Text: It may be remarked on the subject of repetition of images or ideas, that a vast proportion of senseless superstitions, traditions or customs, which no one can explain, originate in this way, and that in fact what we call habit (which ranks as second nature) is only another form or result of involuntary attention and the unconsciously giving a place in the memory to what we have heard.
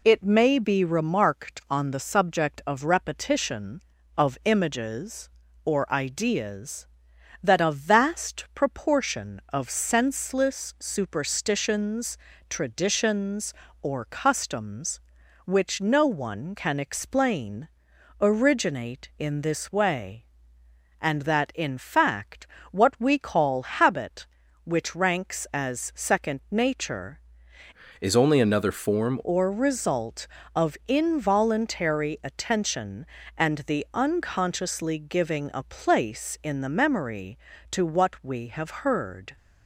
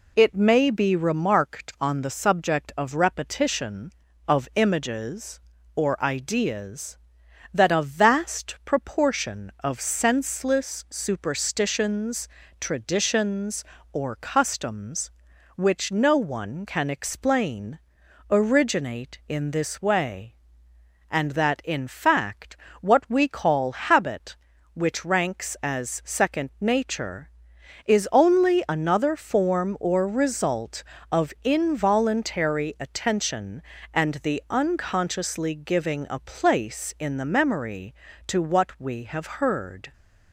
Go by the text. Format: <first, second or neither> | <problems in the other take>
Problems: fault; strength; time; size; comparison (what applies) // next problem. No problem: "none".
second | pauses between "fact" and "what"; slight; at 22.4 s; 0.24 s long; slight in the second // changes voice from "is" to "form"; from 28.0 to 29.2 s; 1.2 s long